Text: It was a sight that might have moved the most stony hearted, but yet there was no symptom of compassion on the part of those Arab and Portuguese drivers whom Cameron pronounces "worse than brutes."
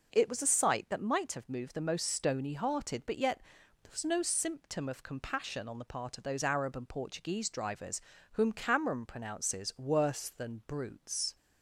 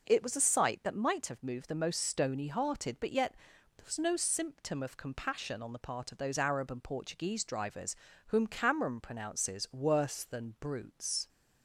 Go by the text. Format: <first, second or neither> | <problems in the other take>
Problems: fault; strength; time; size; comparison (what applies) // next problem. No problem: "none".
neither | pauses between "yet" and "there"; the same in both // pauses between "drivers" and "whom"; slight; the same in both